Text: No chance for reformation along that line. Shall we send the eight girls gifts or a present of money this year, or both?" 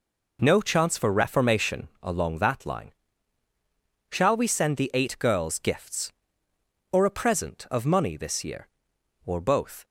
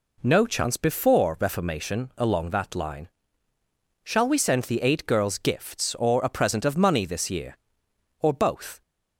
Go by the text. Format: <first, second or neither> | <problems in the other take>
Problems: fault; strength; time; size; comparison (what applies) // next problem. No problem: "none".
first | says "before" for "for"; at 0.7 s